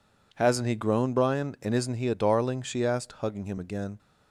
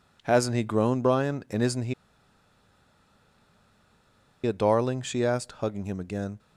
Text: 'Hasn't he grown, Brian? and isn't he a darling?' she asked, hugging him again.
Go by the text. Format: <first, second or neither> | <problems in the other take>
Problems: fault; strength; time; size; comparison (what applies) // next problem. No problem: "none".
first | pauses between "he" and "a"; strong; at 1.9 s; 2.5 s long